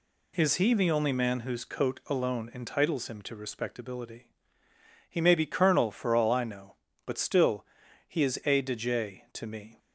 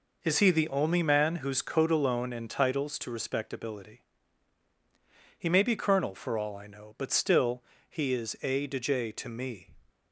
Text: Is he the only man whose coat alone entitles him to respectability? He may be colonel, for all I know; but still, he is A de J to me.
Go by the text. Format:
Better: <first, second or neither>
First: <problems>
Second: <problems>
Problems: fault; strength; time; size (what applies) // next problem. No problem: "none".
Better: first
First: none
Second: skips "him"; at 2.9 s